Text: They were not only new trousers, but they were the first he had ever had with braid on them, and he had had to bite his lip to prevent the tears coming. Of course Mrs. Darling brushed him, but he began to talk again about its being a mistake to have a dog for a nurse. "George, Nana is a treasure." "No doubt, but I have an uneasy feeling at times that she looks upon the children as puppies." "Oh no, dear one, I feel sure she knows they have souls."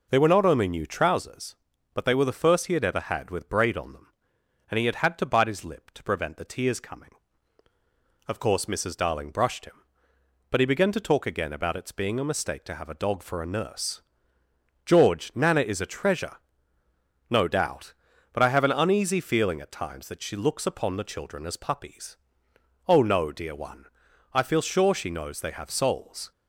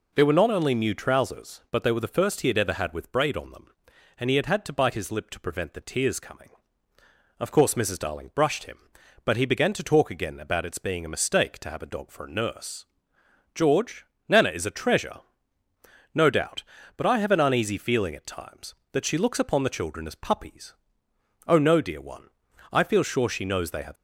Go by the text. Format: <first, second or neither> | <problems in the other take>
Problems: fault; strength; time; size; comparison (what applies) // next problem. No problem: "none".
first | stops before "souls"; at 23.9 s